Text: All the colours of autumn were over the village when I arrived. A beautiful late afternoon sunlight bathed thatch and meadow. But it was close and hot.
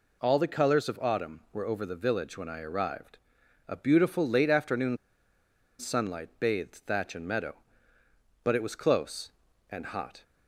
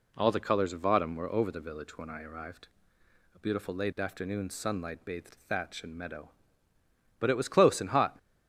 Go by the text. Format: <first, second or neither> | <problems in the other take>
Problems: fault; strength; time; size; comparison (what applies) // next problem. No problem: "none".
second | pauses between "afternoon" and "sunlight"; noticeable; at 4.9 s; 0.82 s long